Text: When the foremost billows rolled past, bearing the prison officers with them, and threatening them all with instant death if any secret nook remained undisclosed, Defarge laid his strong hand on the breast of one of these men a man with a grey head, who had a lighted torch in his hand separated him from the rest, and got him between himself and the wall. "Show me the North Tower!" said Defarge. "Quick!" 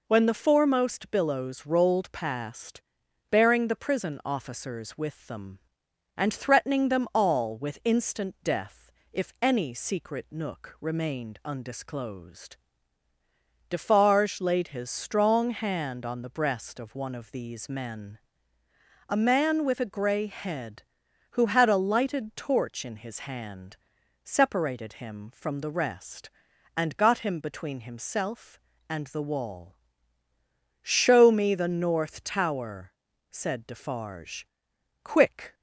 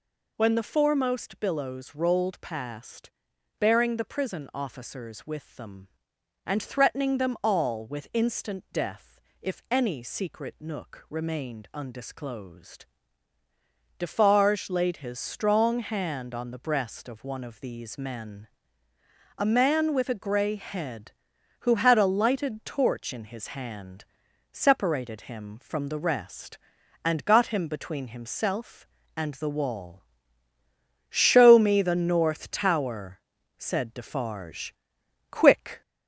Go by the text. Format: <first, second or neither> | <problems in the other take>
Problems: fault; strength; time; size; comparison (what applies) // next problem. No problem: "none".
first | gets louder; slight; throughout; 3 dB // pauses between "death" and "if"; slight; at 9.2 s; 0.22 s long; slight in the first // pauses between "men" and "a"; noticeable; at 18.4 s; 0.90 s long; noticeable in the first // pauses between "hand" and "separated"; noticeable; at 24.0 s; 0.48 s long; noticeable in the first